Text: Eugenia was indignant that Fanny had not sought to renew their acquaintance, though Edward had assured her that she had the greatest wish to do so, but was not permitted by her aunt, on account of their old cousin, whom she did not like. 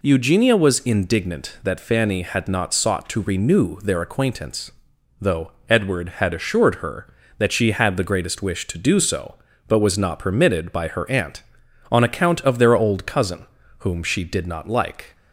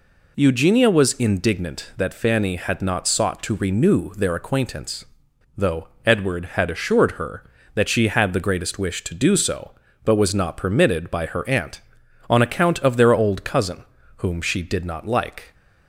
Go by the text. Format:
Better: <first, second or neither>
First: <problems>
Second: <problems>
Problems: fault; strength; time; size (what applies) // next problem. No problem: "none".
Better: neither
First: pauses between "though" and "Edward"; slight; at 5.5 s; 0.18 s long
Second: pauses between "though" and "Edward"; slight; at 5.8 s; 0.18 s long